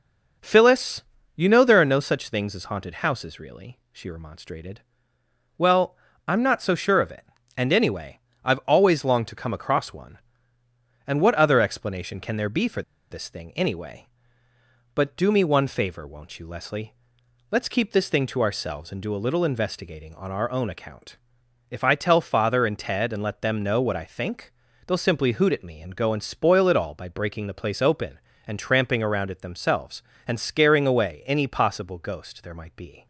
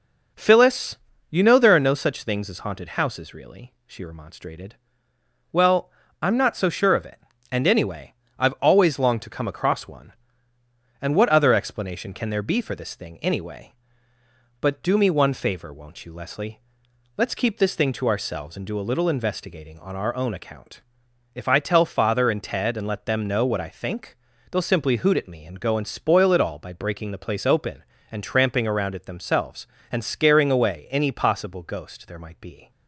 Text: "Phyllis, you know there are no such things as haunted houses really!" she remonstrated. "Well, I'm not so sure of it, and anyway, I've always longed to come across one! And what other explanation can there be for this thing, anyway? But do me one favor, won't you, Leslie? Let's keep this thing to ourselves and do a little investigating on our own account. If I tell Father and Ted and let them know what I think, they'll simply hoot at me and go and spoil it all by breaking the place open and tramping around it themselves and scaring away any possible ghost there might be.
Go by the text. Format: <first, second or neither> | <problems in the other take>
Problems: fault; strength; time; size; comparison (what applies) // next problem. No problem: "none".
second | pauses between "for" and "this"; slight; at 12.8 s; 0.29 s long